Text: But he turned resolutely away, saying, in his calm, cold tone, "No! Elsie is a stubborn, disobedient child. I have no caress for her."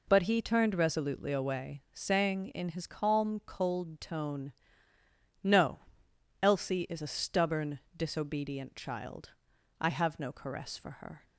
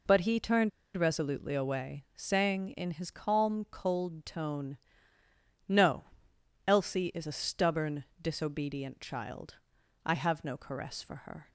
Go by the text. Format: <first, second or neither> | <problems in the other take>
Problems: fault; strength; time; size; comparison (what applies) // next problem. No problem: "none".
first | pauses between "turned" and "resolutely"; slight; at 0.7 s; 0.26 s long